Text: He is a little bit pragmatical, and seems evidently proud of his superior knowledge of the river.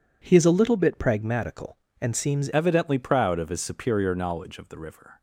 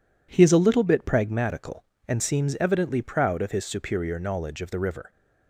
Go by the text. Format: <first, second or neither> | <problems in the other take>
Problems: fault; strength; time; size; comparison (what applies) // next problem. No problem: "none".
second | changes voice at "evidently"; from 2.5 s on; 2.7 s long